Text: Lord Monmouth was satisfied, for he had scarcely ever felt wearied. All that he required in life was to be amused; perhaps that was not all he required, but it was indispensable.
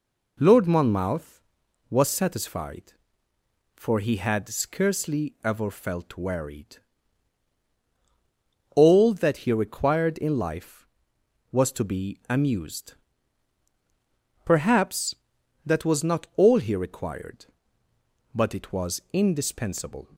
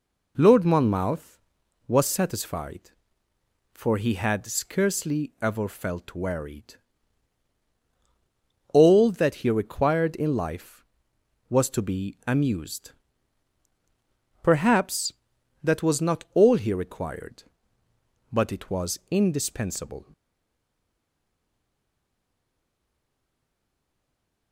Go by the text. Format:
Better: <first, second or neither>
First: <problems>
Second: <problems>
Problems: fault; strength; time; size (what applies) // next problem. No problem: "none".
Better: first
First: none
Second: stays silent after the last word; strong; from 20.1 s on; 4.4 s long